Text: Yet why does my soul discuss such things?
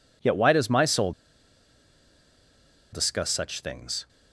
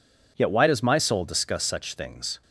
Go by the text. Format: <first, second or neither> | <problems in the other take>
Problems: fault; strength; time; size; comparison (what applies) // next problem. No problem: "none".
second | pauses between "soul" and "discuss"; strong; at 1.1 s; 1.7 s long